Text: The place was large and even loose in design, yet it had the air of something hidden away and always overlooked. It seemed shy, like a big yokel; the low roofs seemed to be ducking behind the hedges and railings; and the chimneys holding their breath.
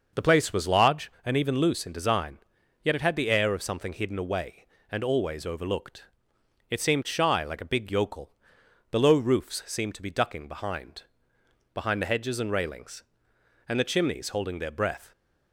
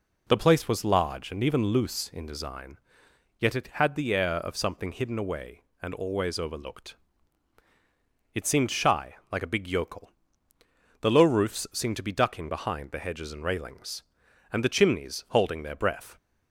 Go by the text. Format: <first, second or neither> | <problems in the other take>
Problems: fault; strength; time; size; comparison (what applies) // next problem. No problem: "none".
second | says "behind" twice; at 11.7 s